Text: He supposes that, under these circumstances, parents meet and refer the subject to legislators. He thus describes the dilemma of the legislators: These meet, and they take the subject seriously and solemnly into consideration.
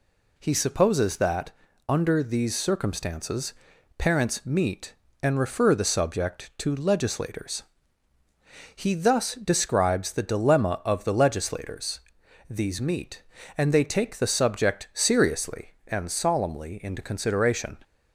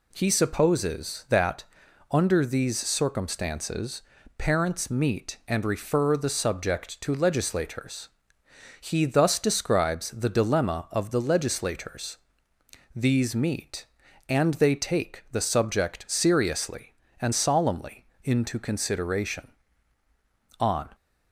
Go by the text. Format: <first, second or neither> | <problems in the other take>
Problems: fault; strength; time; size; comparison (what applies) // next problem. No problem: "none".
first | pauses between "solemnly" and "into"; slight; at 18.0 s; 0.16 s long // goes on to say "On"; slight; from 20.5 s on; 0.30 s long